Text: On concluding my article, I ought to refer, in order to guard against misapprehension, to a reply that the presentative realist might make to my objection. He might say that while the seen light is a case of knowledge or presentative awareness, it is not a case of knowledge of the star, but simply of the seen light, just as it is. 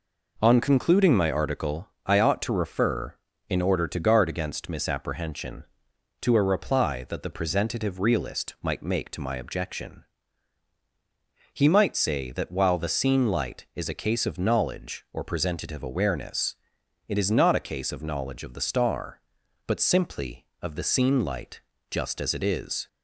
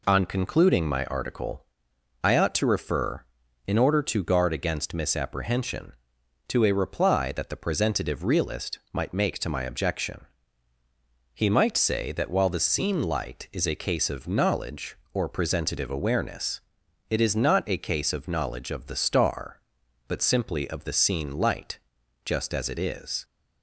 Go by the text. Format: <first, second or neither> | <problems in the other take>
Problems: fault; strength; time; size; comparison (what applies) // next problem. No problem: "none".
neither | none